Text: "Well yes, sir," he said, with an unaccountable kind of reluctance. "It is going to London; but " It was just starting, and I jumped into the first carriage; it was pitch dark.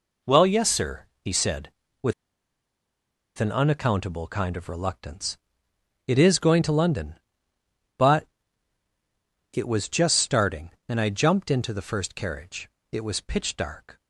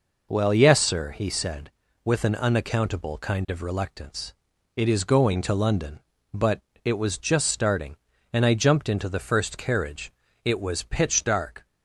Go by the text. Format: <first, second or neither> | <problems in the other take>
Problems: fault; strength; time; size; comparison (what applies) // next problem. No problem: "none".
second | pauses between "with" and "an"; strong; at 2.1 s; 1.2 s long